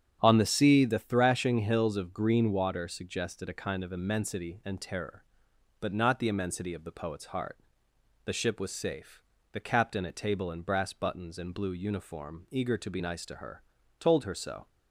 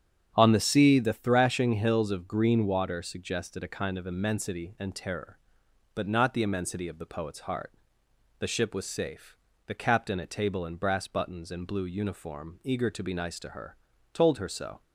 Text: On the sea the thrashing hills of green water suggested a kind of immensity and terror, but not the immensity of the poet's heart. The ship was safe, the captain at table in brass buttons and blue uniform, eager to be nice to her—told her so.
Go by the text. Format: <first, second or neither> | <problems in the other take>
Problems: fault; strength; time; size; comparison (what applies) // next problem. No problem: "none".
neither | starts louder than the rest; strong; the same in both